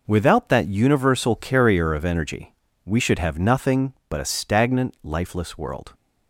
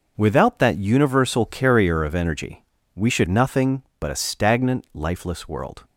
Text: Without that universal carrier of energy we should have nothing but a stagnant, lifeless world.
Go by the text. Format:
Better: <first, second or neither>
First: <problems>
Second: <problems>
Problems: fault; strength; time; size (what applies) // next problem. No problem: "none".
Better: first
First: pauses between "energy" and "we"; slight; at 2.5 s; 0.30 s long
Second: pauses between "energy" and "we"; slight; at 2.6 s; 0.30 s long // skips "have"; at 3.2 s